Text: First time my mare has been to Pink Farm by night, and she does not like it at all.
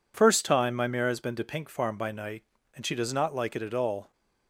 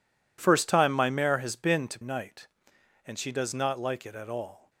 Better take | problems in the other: first | skips "Pink Farm by"; at 2.0 s

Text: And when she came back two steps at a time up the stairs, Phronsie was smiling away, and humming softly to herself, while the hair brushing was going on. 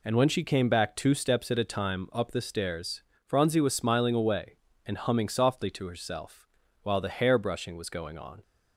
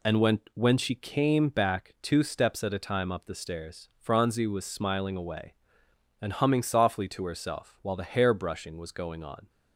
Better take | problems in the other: first | says "when" twice; at 0.5 s

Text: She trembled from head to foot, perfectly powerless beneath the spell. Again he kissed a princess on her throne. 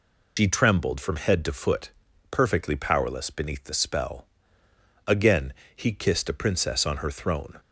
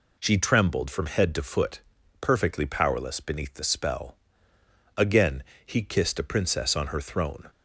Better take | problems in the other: second | loses the start of "She"; at 0.3 s; 85 ms // pauses between "Again" and "he"; slight; at 5.5 s; 0.22 s long; slight in the second

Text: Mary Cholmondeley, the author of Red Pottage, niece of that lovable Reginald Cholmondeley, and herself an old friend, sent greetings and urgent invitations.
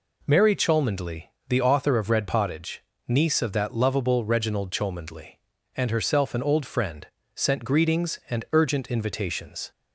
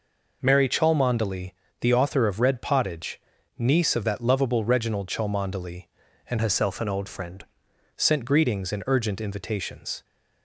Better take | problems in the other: first | changes voice from "herself" to "friend"; from 6.4 to 7.4 s; 1.0 s long

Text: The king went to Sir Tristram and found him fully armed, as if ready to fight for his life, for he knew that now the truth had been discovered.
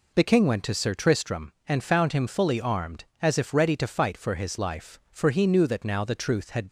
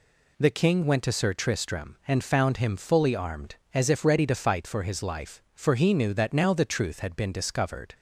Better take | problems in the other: second | stops before "been discovered"; at 6.6 s

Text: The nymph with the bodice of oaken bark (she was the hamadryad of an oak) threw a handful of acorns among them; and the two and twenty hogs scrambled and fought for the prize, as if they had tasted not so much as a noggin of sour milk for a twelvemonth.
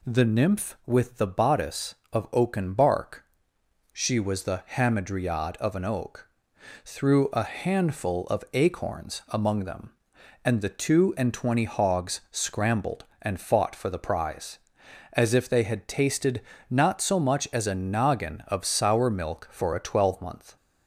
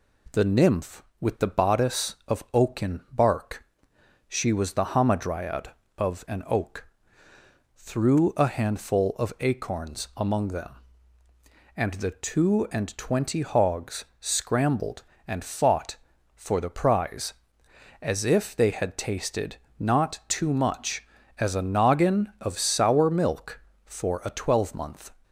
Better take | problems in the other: first | pauses between "hogs" and "scrambled"; slight; at 14.0 s; 0.16 s long // pauses between "tasted" and "not"; slight; at 19.5 s; 0.24 s long; slight in the first // says "too" for "so"; at 20.2 s

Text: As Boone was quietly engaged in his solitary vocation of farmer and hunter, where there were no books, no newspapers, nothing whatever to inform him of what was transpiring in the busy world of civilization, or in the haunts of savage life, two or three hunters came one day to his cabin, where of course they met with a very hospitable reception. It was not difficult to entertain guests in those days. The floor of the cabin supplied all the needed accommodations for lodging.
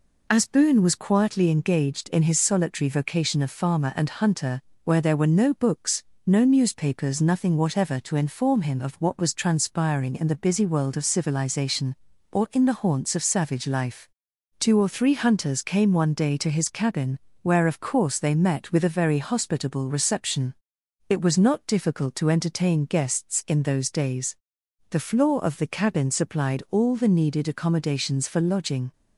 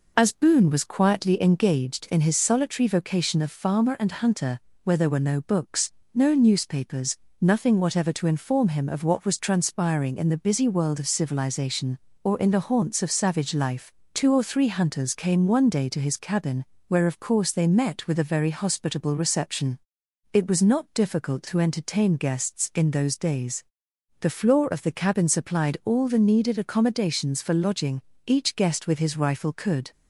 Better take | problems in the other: first | goes on to say "Each guest with his rifle could"; from 28.2 s on; 1.6 s long

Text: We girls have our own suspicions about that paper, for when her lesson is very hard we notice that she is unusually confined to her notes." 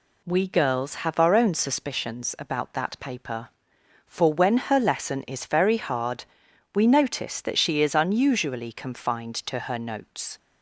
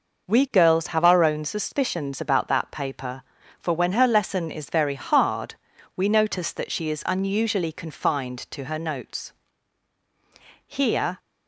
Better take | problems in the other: first | pauses between "hard" and "we"; at 5.5 s; 0.40 s long; noticeable in the first // goes on to say "Here"; from 10.6 s on; 0.52 s long

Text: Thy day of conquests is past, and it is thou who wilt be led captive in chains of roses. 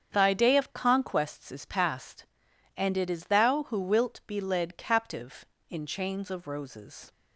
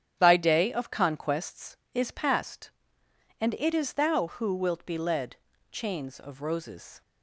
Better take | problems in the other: first | starts louder than the rest; strong; until 1.2 s; 9.5 dB; strong in the first // skips "captive in"; at 5.5 s

